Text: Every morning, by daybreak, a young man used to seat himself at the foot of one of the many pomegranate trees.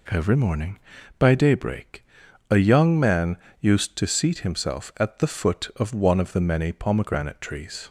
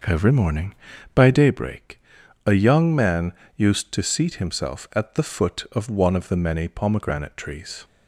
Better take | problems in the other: first | starts louder than the rest; until 1.6 s; 6 dB // pauses between "man" and "used"; slight; at 3.3 s; 0.22 s long; slight in the first

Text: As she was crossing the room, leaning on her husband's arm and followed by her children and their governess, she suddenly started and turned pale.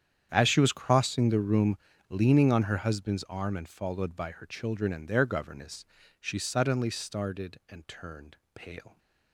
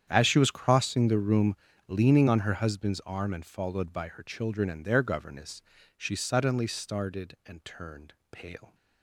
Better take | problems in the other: neither | starts louder than the rest; strong; the same in both // pauses between "turned" and "pale"; slight; the same in both

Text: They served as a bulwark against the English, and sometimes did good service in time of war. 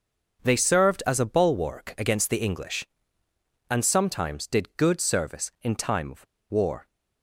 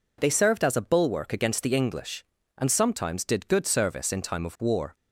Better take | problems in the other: second | starts louder than the rest; until 1.4 s; 6.5 dB // pauses between "of" and "war"; slight; at 6.2 s; 0.25 s long

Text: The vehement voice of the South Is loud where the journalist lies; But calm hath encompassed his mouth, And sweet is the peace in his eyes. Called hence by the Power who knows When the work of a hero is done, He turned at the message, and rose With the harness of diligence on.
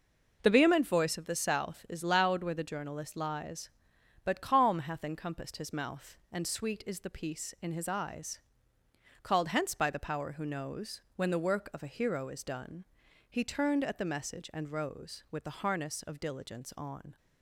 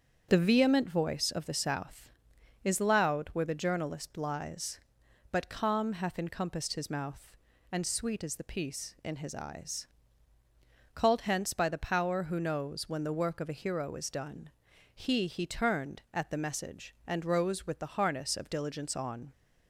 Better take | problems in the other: first | starts louder than the rest; strong; until 1.3 s; 7.5 dB // says "He" twice; at 15.2 s

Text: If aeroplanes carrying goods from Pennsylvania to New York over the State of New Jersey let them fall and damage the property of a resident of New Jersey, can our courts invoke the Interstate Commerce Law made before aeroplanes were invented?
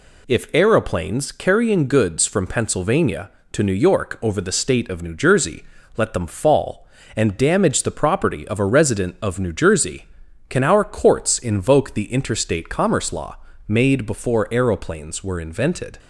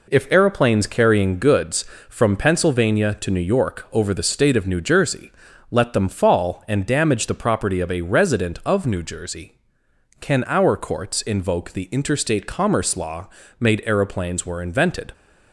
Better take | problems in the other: first | pauses between "Jersey" and "let"; at 5.3 s; 0.40 s long; slight in the first // pauses between "Law" and "made"; slight; at 13.2 s; 0.30 s long; slight in the first // skips "before"; at 13.8 s

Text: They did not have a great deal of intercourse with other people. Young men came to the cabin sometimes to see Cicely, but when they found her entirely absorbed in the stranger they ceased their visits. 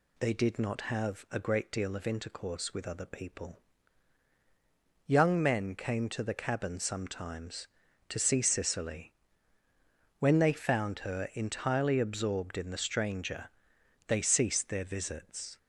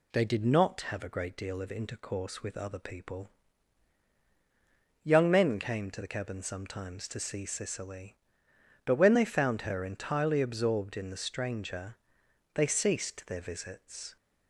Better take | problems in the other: second | skips "but"; at 9.6 s // pauses between "stranger" and "they"; noticeable; at 13.4 s; 0.58 s long; noticeable in the second

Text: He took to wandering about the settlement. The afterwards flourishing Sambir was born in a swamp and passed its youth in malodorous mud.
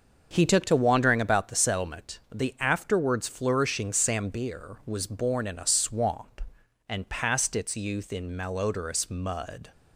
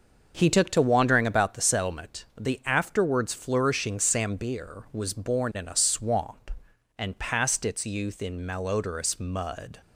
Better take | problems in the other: neither | starts louder than the rest; the same in both

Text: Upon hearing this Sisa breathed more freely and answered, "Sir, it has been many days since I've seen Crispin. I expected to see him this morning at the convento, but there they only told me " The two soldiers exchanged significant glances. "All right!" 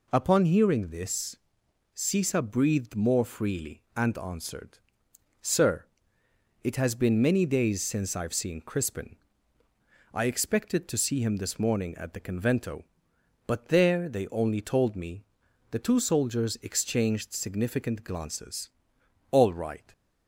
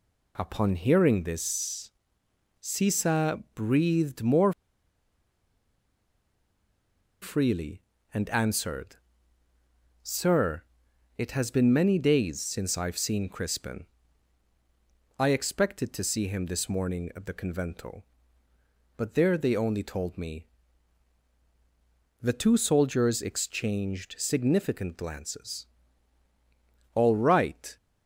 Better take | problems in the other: first | pauses between "this" and "Sisa"; noticeable; at 1.9 s; 0.70 s long; noticeable in the first // pauses between "more" and "freely"; strong; at 4.5 s; 2.6 s long

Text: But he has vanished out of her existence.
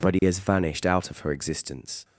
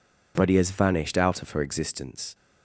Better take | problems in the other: neither | none

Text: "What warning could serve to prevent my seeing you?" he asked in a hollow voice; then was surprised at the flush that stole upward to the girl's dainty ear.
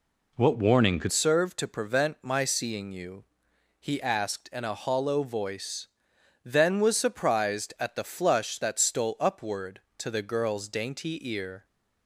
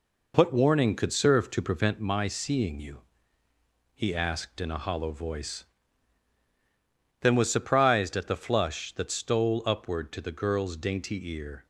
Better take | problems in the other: second | changes voice at "serve"; from 1.1 s on; 10.5 s long

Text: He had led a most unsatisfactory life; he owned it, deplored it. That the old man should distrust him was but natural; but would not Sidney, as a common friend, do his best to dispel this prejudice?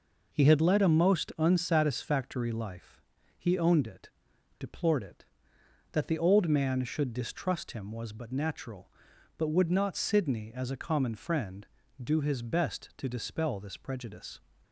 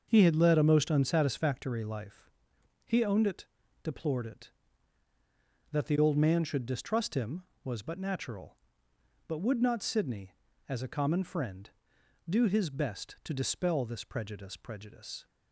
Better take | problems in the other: first | starts louder than the rest; until 1.1 s; 6.5 dB // says "prejudice" twice; at 14.5 s

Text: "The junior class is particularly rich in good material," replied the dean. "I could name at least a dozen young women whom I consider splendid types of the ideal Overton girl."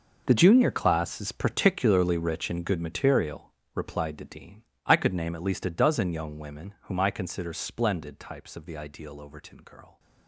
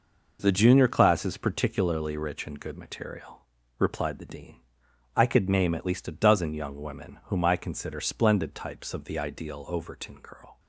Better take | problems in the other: second | gets quieter; strong; throughout; 15 dB

